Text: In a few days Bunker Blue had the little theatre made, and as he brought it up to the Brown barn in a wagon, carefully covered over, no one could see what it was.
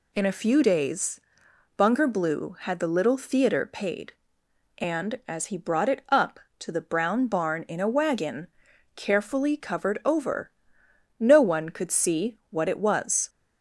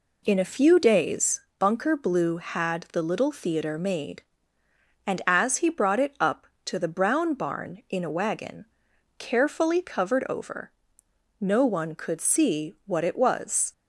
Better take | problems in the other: second | pauses between "days" and "Bunker"; noticeable; at 1.2 s; 0.56 s long; slight in the second // says "paid" for "made"; at 3.6 s

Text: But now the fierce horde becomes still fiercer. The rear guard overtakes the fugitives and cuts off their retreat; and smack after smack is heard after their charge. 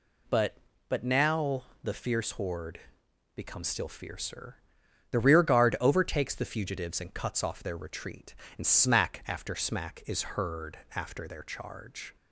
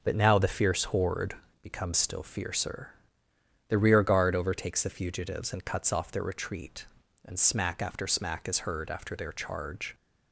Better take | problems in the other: second | says "But" twice; at 0.8 s // pauses between "now" and "the"; slight; at 1.6 s; 0.20 s long // pauses between "horde" and "becomes"; noticeable; at 2.7 s; 0.54 s long; slight in the second // pauses between "heard" and "after"; slight; at 10.7 s; 0.18 s long

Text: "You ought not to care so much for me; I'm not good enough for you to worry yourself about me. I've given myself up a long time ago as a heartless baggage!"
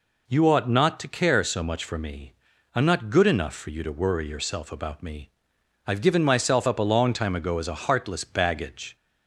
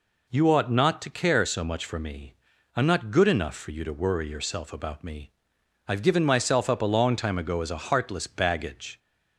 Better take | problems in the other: neither | none

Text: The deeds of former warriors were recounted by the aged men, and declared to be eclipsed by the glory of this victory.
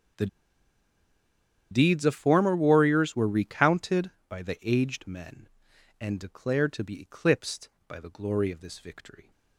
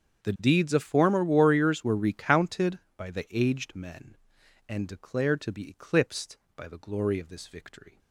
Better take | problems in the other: second | starts louder than the rest; strong; until 2.6 s; 7.5 dB; strong in the second // pauses between "The" and "deeds"; strong; at 0.2 s; 1.4 s long

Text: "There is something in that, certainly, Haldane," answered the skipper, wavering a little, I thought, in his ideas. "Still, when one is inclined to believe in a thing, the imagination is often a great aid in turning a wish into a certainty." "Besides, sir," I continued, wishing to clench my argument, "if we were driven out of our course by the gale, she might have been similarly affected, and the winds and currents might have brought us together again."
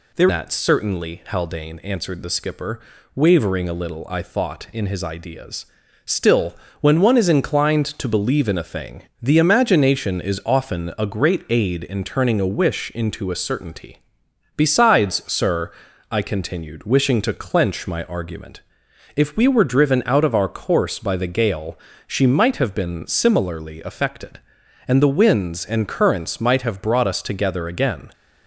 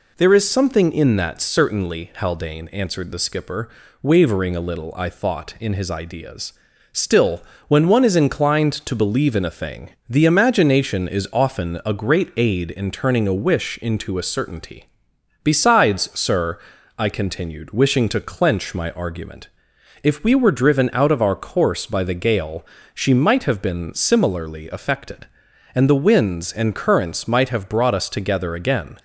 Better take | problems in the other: second | skips "is something in"; at 0.2 s

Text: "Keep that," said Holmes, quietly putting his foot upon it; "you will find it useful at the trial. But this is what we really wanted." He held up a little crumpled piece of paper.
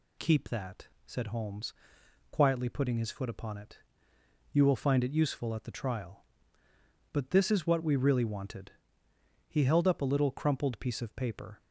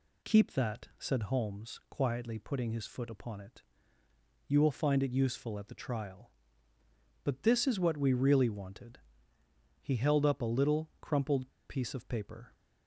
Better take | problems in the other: first | pauses between "crumpled" and "piece"; slight; at 11.4 s; 0.21 s long

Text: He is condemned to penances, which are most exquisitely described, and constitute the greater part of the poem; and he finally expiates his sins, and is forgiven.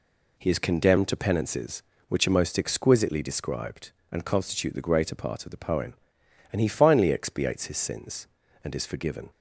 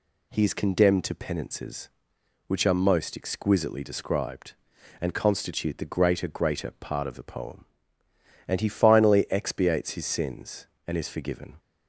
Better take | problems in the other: first | says "greater" twice; at 6.2 s

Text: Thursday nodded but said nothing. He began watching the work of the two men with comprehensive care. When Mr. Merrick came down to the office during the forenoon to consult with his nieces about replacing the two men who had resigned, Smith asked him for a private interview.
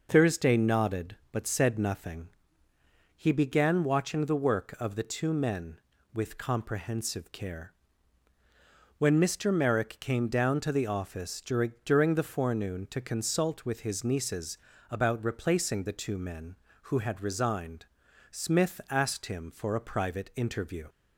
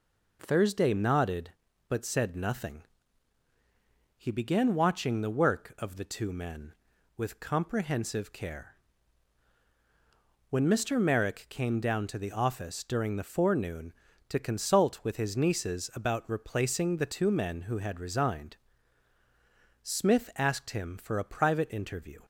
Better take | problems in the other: second | says "during" twice; at 11.8 s // pauses between "nieces" and "about"; slight; at 14.5 s; 0.32 s long

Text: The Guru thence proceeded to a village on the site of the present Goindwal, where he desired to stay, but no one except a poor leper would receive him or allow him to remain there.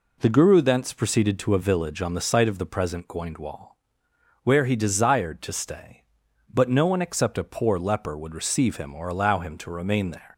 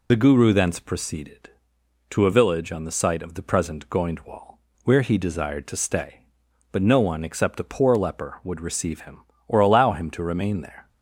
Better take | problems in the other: first | loses the start of "The"; at 0.0 s; 50 ms

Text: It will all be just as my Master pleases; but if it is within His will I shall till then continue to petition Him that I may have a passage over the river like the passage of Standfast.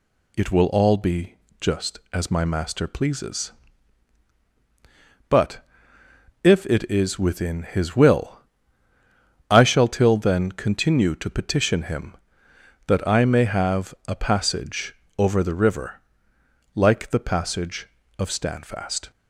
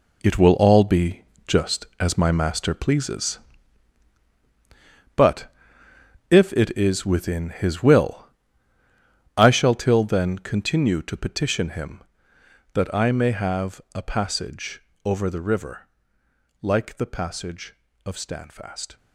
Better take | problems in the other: first | gets quieter; strong; throughout; 10.5 dB // pauses between "be" and "just"; slight; at 1.2 s; 0.24 s long; slight in the first // pauses between "but" and "if"; noticeable; at 5.4 s; 0.82 s long; noticeable in the first // pauses between "will" and "I"; at 8.2 s; 1.1 s long; also in the first // pauses between "have" and "a"; slight; at 13.7 s; 0.16 s long; slight in the first // pauses between "passage" and "over"; slight; at 14.8 s; 0.24 s long; slight in the first // pauses between "river" and "like"; noticeable; at 15.8 s; 0.74 s long; noticeable in the first

